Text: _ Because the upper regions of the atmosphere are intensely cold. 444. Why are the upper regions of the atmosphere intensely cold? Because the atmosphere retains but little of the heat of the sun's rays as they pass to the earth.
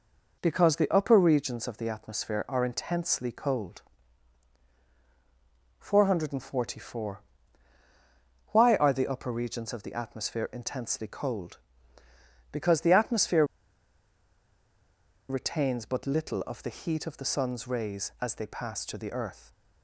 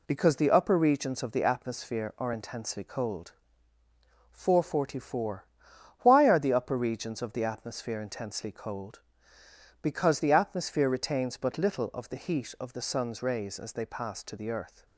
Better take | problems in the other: second | pauses between "atmosphere" and "retains"; strong; at 13.4 s; 1.8 s long

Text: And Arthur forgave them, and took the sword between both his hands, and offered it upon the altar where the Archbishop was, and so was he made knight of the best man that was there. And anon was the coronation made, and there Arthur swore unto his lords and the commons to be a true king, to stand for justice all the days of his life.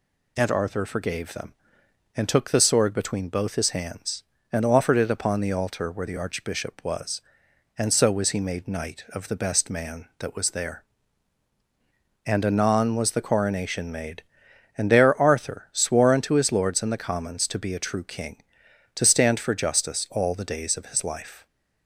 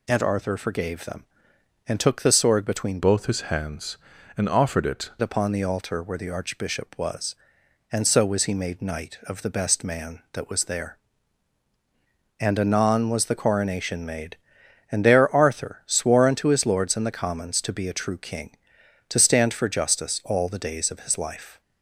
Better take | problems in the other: first | changes voice from "both" to "it"; from 3.0 to 5.1 s; 2.1 s long

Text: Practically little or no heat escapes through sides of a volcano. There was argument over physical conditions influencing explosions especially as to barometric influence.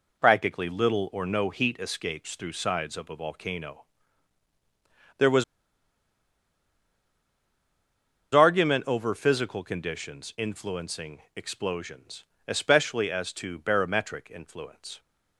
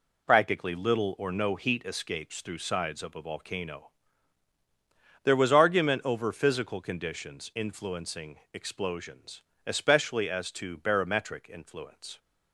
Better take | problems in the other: second | pauses between "was" and "argument"; strong; at 5.4 s; 2.8 s long // pauses between "explosions" and "especially"; slight; at 12.2 s; 0.24 s long; slight in the second

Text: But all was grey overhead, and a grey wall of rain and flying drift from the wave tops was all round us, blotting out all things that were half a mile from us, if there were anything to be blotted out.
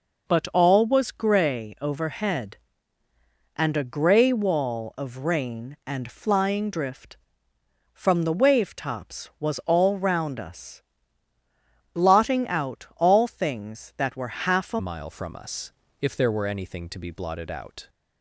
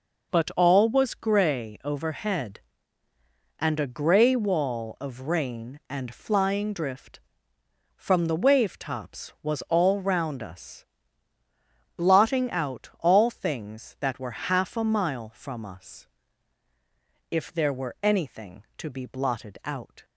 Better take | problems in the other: second | changes voice at "mile"; from 14.7 s on; 3.1 s long

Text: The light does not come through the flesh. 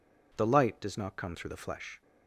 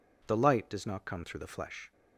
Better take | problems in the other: neither | none

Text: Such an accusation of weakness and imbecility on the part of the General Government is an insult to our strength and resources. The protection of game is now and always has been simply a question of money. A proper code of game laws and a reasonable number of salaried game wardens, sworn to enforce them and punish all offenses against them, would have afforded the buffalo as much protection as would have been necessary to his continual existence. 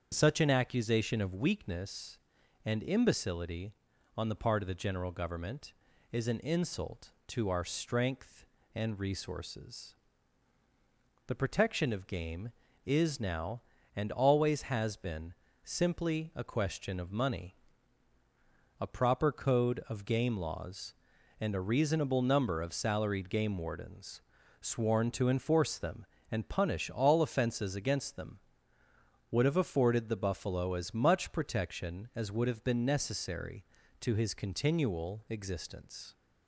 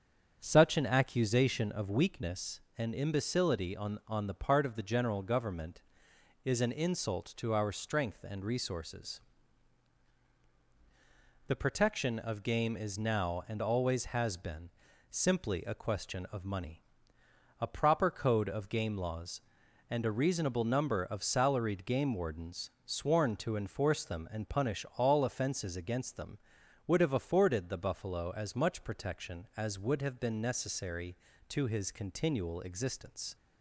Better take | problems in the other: first | starts louder than the rest; strong; until 1.4 s; 7.5 dB; strong in the first // says "on" twice; at 4.0 s // pauses between "been" and "simply"; at 14.6 s; 0.42 s long; slight in the first

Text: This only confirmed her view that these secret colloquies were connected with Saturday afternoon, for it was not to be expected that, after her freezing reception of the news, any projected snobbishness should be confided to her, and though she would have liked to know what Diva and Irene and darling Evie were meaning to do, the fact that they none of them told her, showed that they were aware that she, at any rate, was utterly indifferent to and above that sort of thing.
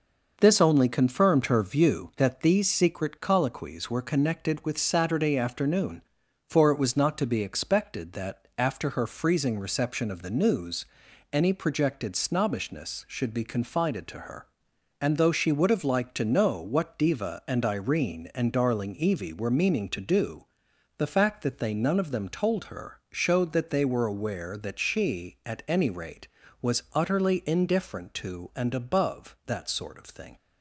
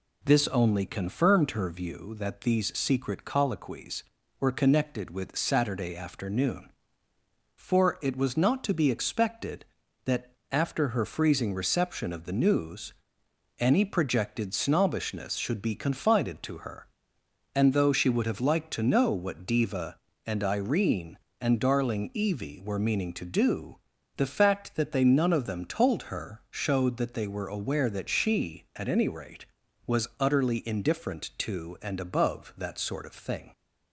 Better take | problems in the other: neither | none

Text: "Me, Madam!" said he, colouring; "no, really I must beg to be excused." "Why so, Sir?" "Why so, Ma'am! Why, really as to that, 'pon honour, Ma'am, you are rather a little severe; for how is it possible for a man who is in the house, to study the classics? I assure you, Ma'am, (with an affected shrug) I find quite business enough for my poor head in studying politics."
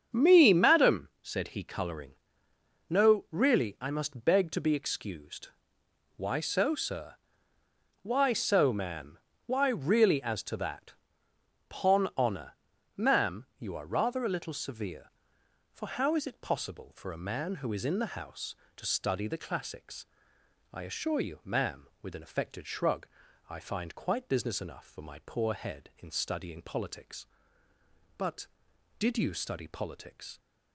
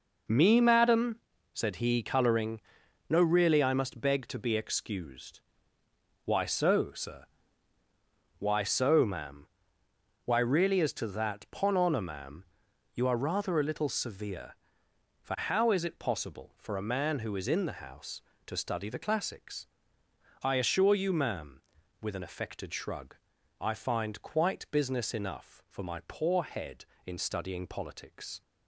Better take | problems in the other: second | starts louder than the rest; strong; until 1.2 s; 7.5 dB // goes on to say "But did you study politics"; strong; from 28.1 s on; 2.2 s long

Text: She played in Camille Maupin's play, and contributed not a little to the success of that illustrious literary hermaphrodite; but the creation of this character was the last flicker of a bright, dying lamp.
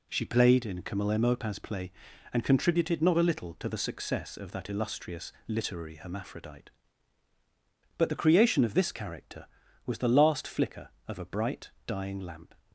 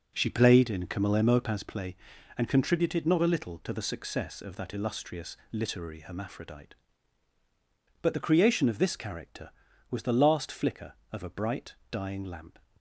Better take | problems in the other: first | starts louder than the rest; noticeable; until 1.7 s; 5 dB

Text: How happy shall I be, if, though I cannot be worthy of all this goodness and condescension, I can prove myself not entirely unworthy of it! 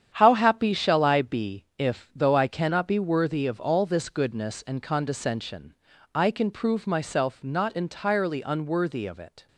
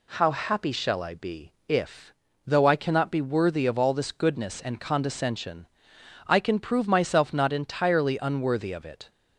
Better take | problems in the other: second | gets quieter; strong; throughout; 9 dB

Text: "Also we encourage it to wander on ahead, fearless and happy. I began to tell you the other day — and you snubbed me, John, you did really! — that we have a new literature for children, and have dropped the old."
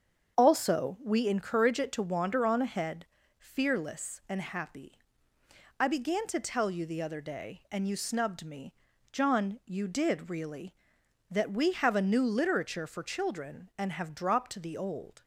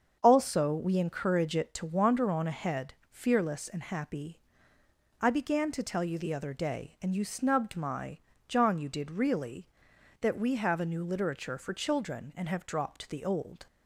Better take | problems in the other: first | starts louder than the rest; until 1.2 s; 7 dB; strong in the first // says "my" for "me"; at 7.7 s

